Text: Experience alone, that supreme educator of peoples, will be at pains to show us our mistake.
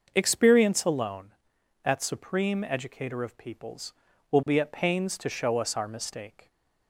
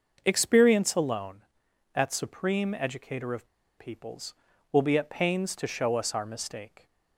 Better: first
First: starts louder than the rest; noticeable; until 1.1 s; 6 dB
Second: starts louder than the rest; noticeable; until 1.2 s; 6 dB // pauses between "of" and "peoples"; slight; at 3.4 s; 0.30 s long

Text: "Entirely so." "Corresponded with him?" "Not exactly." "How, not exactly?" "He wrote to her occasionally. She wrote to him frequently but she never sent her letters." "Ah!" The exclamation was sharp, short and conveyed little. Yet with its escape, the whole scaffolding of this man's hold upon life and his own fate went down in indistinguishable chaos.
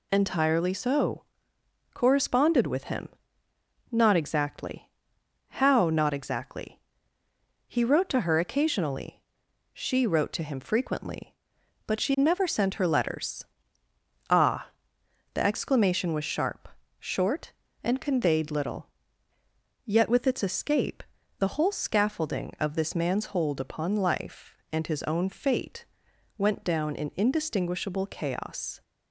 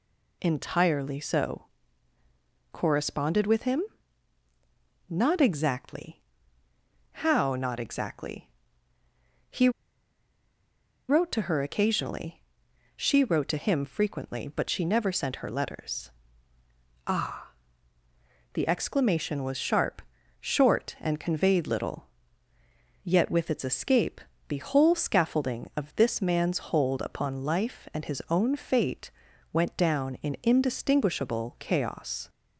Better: first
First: pauses between "fate" and "went"; noticeable; at 25.8 s; 0.50 s long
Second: pauses between "He" and "wrote"; strong; at 9.6 s; 1.3 s long // pauses between "fate" and "went"; at 29.0 s; 0.44 s long

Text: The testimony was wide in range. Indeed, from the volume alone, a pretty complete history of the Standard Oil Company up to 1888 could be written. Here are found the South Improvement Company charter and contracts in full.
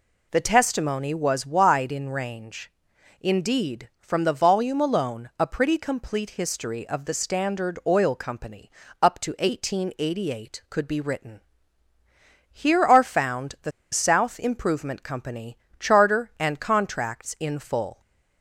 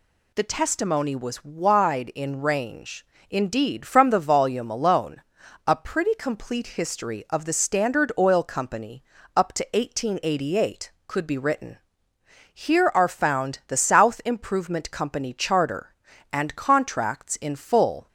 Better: second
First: pauses between "Company" and "up"; slight; at 8.6 s; 0.32 s long // pauses between "the" and "South"; slight; at 13.7 s; 0.20 s long // pauses between "Company" and "charter"; slight; at 15.5 s; 0.22 s long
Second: pauses between "Company" and "up"; slight; at 9.0 s; 0.32 s long

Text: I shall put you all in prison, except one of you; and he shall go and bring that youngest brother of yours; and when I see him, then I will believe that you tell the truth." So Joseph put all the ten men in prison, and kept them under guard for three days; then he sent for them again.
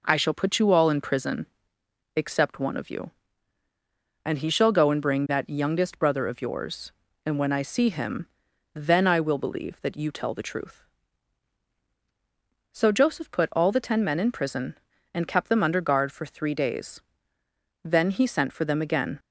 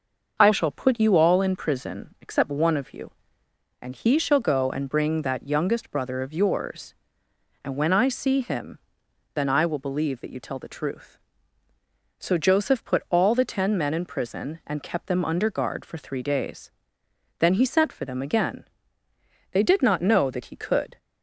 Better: first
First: none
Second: starts louder than the rest; until 1.4 s; 6 dB // goes on to say "They did not know that he could"; from 19.5 s on; 1.4 s long

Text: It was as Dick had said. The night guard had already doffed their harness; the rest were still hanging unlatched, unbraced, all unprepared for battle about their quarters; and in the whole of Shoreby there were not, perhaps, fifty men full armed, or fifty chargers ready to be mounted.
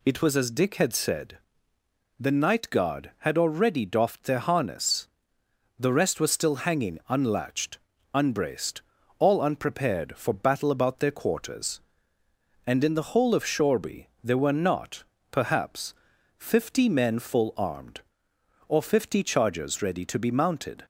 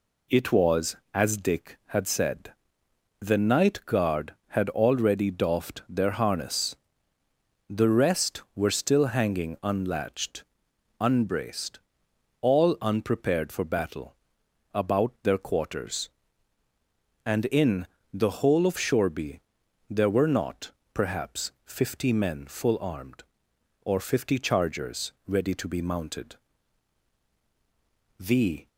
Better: first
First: pauses between "Shoreby" and "there"; slight; at 14.0 s; 0.18 s long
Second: pauses between "battle" and "about"; noticeable; at 14.1 s; 0.58 s long // pauses between "in" and "the"; slight; at 17.8 s; 0.26 s long // pauses between "Shoreby" and "there"; noticeable; at 19.3 s; 0.50 s long // goes on to say "The"; slight; from 28.1 s on; 0.48 s long

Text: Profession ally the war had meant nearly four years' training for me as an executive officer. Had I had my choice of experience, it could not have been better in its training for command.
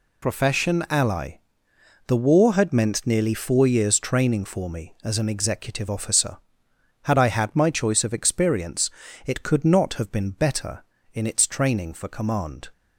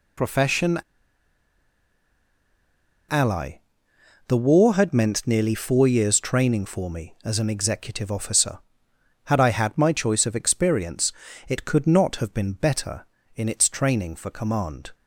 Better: first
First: pauses between "ally" and "the"; noticeable; at 1.3 s; 0.68 s long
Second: pauses between "Profession" and "ally"; strong; at 0.8 s; 2.2 s long // pauses between "ally" and "the"; noticeable; at 3.5 s; 0.68 s long

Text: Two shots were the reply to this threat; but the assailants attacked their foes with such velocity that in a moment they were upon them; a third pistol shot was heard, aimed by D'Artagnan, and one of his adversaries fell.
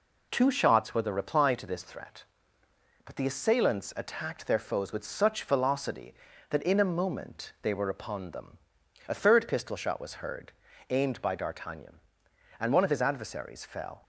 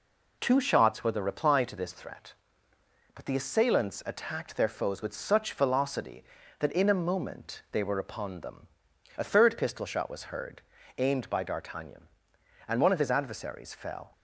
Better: neither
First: none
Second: none

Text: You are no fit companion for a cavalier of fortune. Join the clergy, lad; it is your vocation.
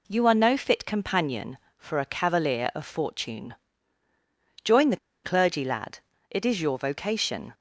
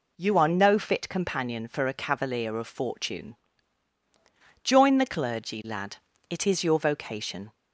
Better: second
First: pauses between "the" and "clergy"; slight; at 4.9 s; 0.26 s long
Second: none

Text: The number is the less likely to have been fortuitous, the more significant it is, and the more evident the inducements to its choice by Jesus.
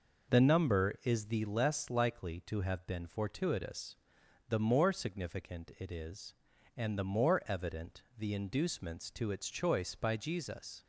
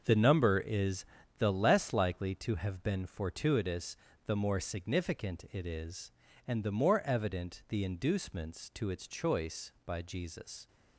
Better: first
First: none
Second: gets quieter; strong; throughout; 9.5 dB // pauses between "is" and "the"; slight; at 1.0 s; 0.32 s long

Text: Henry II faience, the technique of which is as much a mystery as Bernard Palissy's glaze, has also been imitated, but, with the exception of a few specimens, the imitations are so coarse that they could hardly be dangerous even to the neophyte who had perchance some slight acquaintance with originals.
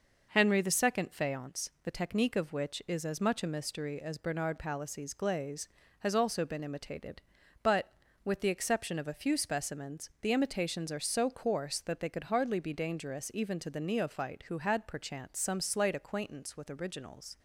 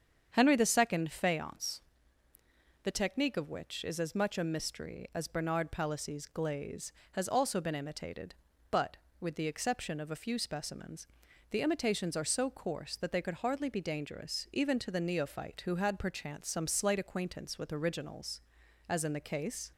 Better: first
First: none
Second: starts louder than the rest; strong; until 1.3 s; 7.5 dB // goes on to say "As in the case"; noticeable; from 18.8 s on; 0.84 s long

